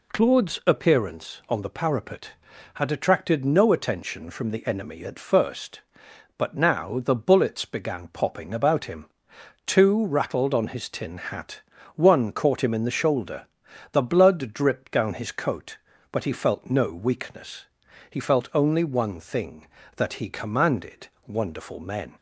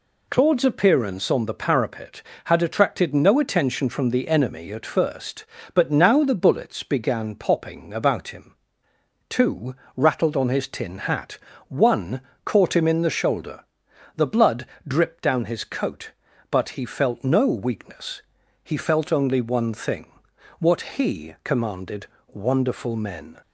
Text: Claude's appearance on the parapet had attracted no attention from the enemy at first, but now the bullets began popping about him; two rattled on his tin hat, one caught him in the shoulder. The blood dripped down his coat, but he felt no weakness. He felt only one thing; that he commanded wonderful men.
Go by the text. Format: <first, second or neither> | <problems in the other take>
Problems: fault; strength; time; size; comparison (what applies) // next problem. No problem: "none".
first | pauses between "two" and "rattled"; slight; at 9.7 s; 0.22 s long // pauses between "one" and "caught"; slight; at 12.2 s; 0.24 s long // pauses between "blood" and "dripped"; slight; at 14.6 s; 0.20 s long // says "what" for "that"; at 20.5 s // pauses between "commanded" and "wonderful"; slight; at 22.0 s; 0.30 s long; slight in the first